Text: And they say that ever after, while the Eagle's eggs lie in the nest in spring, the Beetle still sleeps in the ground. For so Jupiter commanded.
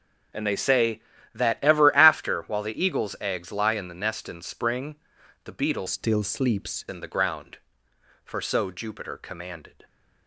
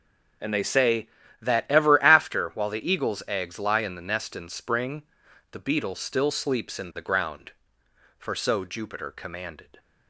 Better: second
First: starts louder than the rest; strong; until 1.7 s; 7.5 dB // changes voice from "still" to "sleeps"; from 5.8 to 6.8 s; 1.0 s long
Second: starts louder than the rest; until 1.7 s; 7 dB

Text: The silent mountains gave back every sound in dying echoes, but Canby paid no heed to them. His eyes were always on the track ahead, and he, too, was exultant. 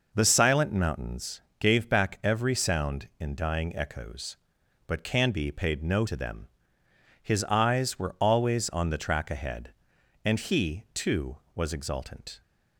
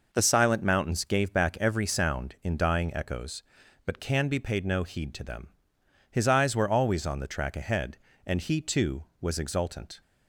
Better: second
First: pauses between "mountains" and "gave"; slight; at 1.4 s; 0.18 s long // skips "heed"; at 6.0 s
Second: none

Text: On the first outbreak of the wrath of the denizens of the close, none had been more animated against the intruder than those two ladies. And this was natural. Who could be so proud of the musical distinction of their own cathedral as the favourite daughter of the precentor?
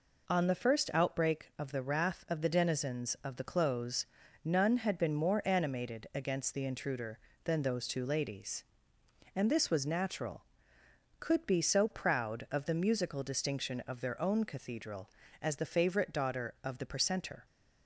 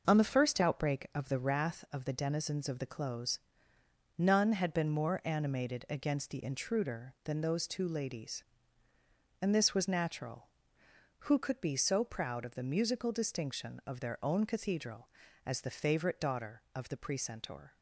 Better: second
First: skips "Who"; at 10.8 s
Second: none

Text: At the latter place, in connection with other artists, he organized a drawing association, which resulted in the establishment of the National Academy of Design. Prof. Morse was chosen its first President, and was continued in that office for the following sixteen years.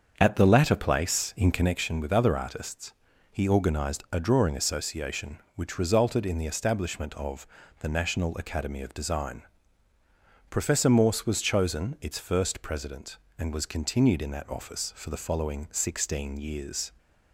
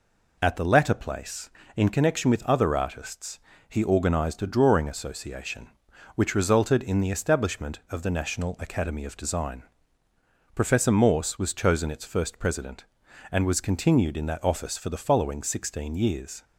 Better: second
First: starts louder than the rest; until 1.9 s; 7 dB // pauses between "of" and "the"; slight; at 7.4 s; 0.36 s long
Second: none

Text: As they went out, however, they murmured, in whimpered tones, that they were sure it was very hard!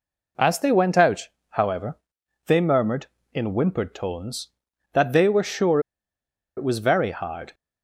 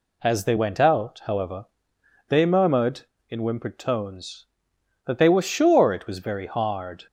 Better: second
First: pauses between "sure" and "it"; noticeable; at 5.7 s; 0.77 s long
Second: none

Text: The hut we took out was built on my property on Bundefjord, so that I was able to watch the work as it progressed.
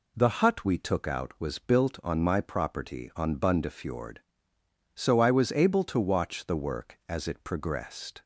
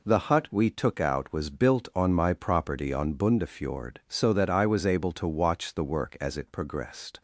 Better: second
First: skips "that"; at 5.1 s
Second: none

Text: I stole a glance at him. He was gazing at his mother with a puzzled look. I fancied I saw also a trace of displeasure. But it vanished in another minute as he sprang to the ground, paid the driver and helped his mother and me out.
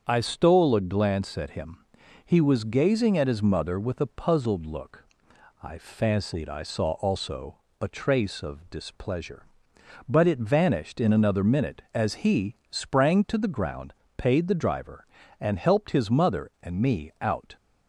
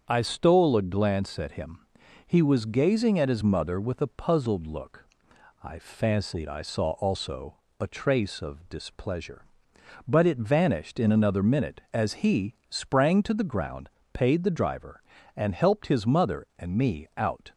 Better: neither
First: starts louder than the rest; strong; until 1.0 s; 7 dB // pauses between "also" and "a"; slight; at 7.5 s; 0.20 s long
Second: starts louder than the rest; strong; until 1.0 s; 7 dB // pauses between "also" and "a"; slight; at 7.5 s; 0.20 s long

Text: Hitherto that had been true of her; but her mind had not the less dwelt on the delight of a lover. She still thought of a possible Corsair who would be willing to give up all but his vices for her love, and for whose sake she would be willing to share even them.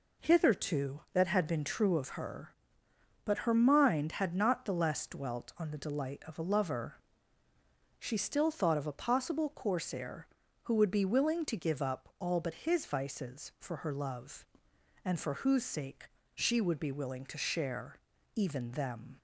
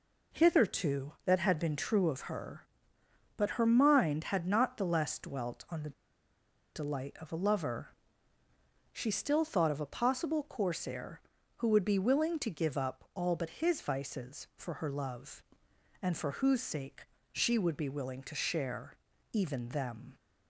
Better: first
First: pauses between "sake" and "she"; slight; at 16.0 s; 0.26 s long // pauses between "share" and "even"; at 17.9 s; 0.38 s long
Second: pauses between "the" and "delight"; noticeable; at 5.9 s; 0.83 s long // pauses between "sake" and "she"; slight; at 17.0 s; 0.26 s long // pauses between "share" and "even"; at 18.9 s; 0.38 s long

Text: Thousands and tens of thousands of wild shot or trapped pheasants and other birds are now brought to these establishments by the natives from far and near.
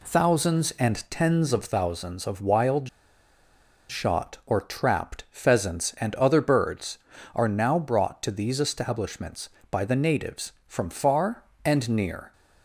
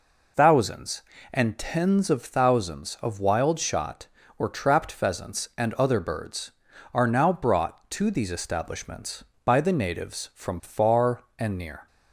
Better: second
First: pauses between "wild" and "shot"; at 2.8 s; 1.0 s long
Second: none

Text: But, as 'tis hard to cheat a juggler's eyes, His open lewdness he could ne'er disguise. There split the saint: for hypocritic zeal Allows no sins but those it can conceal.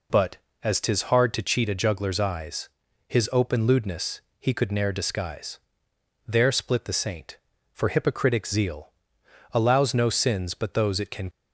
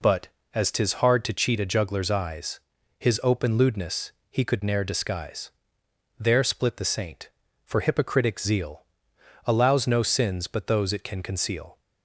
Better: second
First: pauses between "lewdness" and "he"; slight; at 4.2 s; 0.18 s long // pauses between "zeal" and "Allows"; noticeable; at 8.9 s; 0.60 s long // stops before "conceal"; at 11.3 s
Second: pauses between "lewdness" and "he"; slight; at 4.1 s; 0.18 s long // pauses between "zeal" and "Allows"; noticeable; at 8.8 s; 0.60 s long

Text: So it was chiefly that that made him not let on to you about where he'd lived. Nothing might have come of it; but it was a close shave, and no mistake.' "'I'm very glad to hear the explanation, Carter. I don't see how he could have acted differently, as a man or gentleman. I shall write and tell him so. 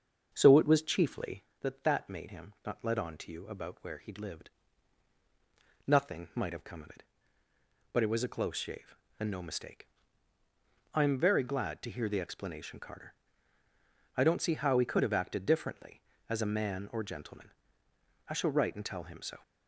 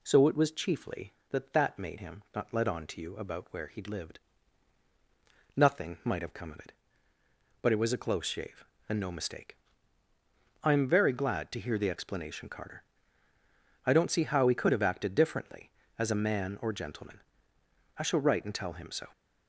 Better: second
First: starts louder than the rest; until 1.4 s; 7 dB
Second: none

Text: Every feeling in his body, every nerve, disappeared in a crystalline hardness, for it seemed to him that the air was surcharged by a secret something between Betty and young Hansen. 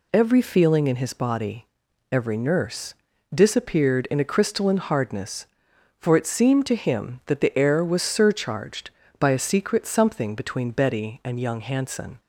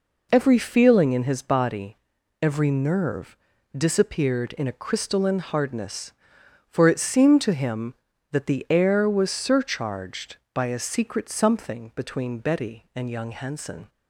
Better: second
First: says "nurse" for "nerve"; at 2.3 s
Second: none

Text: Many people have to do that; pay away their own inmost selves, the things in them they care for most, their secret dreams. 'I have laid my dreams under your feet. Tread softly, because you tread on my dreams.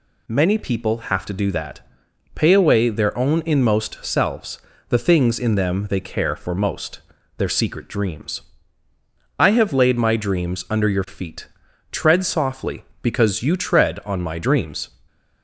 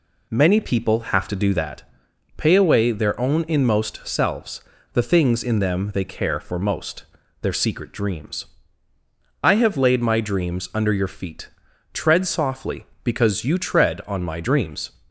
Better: first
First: none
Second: starts louder than the rest; slight; until 1.8 s; 2.5 dB

